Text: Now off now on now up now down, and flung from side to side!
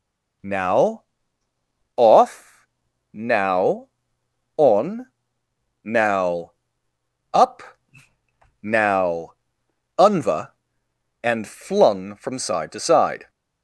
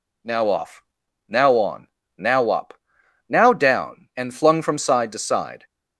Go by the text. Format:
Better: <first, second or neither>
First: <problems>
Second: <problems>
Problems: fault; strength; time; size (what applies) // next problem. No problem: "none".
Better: second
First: pauses between "Now" and "off"; noticeable; at 1.0 s; 0.94 s long // pauses between "off" and "now"; at 2.6 s; 0.44 s long // pauses between "on" and "now"; noticeable; at 5.0 s; 0.76 s long // pauses between "now" and "up"; noticeable; at 6.5 s; 0.82 s long // pauses between "up" and "now"; at 7.6 s; 1.0 s long // says "unva" for "down"; at 9.9 s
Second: pauses between "off" and "now"; noticeable; at 0.8 s; 0.46 s long // pauses between "on" and "now"; slight; at 1.8 s; 0.32 s long // pauses between "up" and "now"; noticeable; at 2.7 s; 0.52 s long